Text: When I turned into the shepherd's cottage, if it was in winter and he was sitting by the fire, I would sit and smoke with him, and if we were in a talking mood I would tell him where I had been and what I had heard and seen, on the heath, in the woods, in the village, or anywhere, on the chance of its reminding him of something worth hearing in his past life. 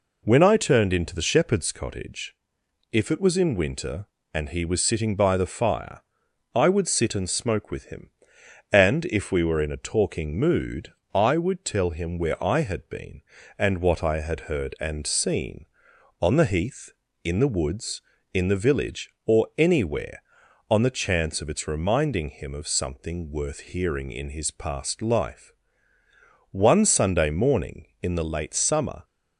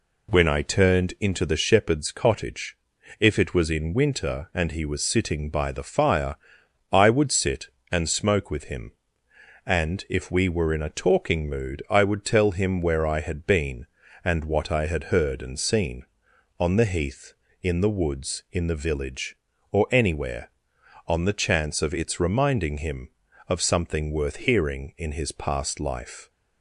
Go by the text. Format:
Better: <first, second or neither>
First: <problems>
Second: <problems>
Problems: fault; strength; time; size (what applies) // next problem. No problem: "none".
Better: second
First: pauses between "mood" and "I"; slight; at 10.9 s; 0.20 s long // goes on to say "One Sunday morning in the late summer"; strong; from 26.4 s on; 2.5 s long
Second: none